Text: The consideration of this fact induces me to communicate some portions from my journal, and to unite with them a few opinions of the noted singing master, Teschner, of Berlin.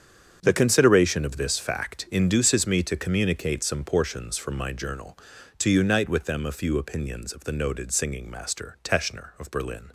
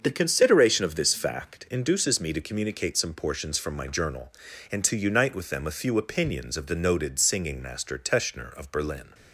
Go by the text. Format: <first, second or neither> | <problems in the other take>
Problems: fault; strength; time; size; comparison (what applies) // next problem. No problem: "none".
second | starts louder than the rest; strong; until 1.4 s; 8 dB; also in the second // skips "and"; at 5.3 s